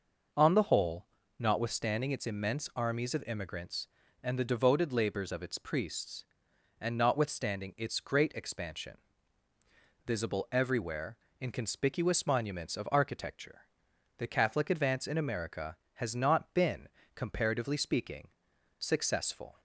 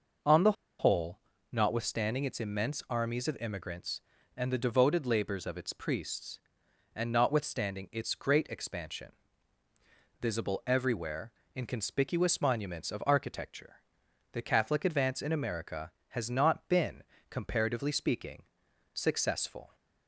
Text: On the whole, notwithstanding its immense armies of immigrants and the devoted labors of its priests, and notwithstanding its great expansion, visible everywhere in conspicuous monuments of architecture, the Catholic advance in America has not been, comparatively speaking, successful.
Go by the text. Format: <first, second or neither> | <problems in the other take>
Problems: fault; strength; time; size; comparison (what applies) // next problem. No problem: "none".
first | pauses between "the" and "whole"; slight; at 0.5 s; 0.26 s long